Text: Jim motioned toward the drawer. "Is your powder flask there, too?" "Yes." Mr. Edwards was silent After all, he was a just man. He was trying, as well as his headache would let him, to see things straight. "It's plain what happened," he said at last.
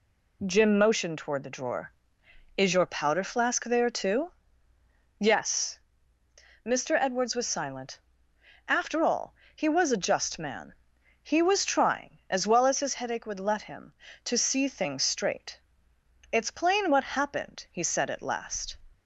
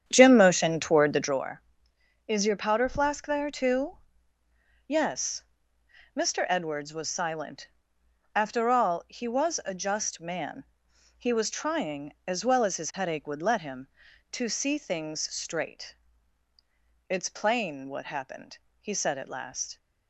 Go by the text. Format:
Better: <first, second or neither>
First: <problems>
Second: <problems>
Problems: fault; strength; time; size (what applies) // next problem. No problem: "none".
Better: first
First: pauses between "silent" and "After"; noticeable; at 7.9 s; 0.68 s long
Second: starts louder than the rest; strong; until 1.5 s; 9 dB // pauses between "silent" and "After"; noticeable; at 7.6 s; 0.66 s long